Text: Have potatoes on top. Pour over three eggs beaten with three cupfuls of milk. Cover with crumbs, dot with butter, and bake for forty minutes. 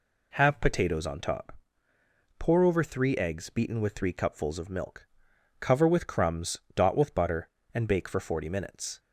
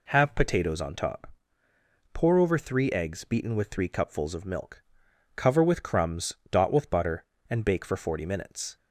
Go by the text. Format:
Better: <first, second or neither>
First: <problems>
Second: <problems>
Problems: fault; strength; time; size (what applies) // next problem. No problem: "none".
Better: neither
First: none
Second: none